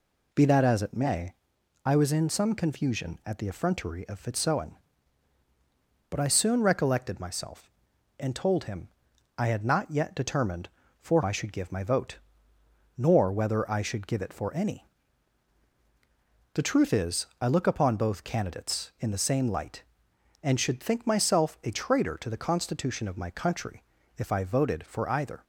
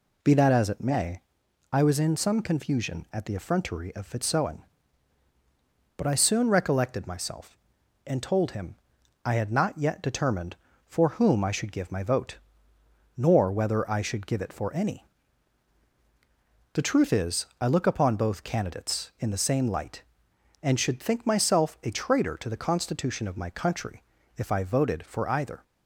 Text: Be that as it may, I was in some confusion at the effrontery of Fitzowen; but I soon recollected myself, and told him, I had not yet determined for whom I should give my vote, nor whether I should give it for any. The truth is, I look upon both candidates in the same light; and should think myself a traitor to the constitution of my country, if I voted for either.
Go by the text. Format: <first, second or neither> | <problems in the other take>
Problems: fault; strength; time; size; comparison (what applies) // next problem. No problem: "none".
second | skips "whom"; at 11.2 s